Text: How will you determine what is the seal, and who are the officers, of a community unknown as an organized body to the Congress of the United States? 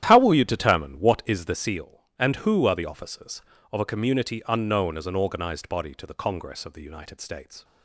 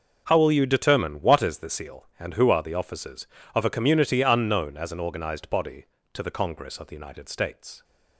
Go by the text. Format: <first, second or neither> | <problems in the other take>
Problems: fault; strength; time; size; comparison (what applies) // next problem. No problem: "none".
second | starts louder than the rest; strong; until 1.6 s; 11.5 dB